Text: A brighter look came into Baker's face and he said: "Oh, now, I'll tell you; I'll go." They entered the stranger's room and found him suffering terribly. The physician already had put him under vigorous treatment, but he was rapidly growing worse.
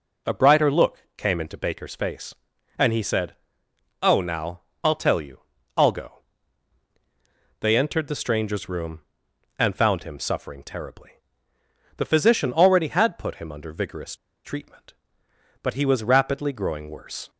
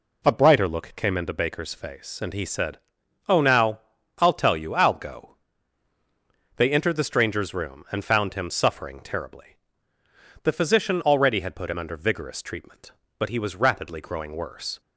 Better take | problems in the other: second | pauses between "look" and "came"; slight; at 0.9 s; 0.18 s long // pauses between "vigorous" and "treatment"; slight; at 14.1 s; 0.30 s long

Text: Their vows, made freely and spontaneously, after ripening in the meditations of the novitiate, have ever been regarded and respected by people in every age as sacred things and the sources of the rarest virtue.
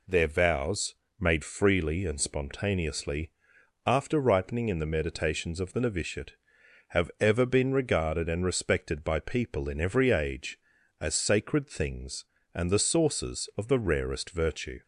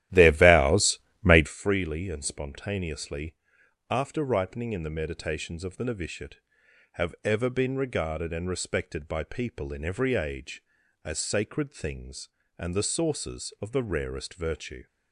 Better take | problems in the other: first | starts louder than the rest; strong; until 1.5 s; 13.5 dB

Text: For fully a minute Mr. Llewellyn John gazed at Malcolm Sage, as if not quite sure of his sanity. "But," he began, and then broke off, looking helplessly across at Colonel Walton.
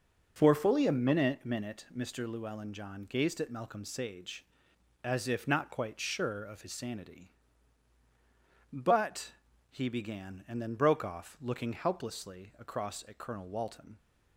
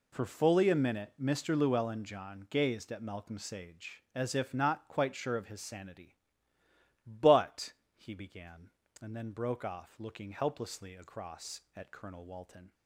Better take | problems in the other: second | says "minute" twice; at 1.4 s

